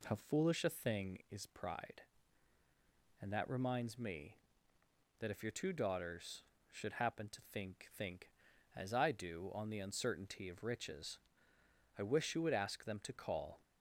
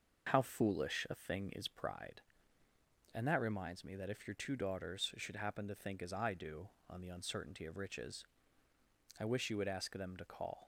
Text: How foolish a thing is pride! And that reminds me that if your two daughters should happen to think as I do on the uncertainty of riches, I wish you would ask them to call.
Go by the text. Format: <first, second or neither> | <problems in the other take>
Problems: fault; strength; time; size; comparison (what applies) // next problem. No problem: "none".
second | says "think" twice; at 7.9 s